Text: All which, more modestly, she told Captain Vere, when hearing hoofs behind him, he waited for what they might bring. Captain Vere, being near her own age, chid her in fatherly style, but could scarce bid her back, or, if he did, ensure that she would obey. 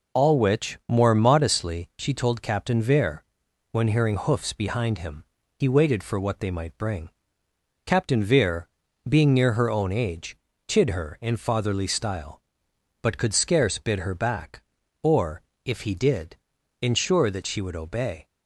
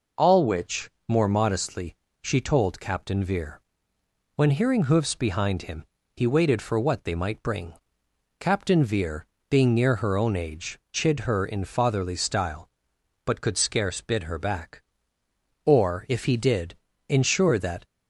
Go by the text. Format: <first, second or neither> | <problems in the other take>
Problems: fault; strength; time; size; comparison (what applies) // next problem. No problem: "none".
first | stops before "she would obey"; at 17.8 s